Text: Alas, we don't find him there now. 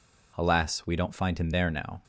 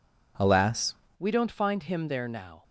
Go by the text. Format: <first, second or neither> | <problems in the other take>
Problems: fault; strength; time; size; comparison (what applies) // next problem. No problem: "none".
first | changes voice at "we"; from 1.1 s on; 1.5 s long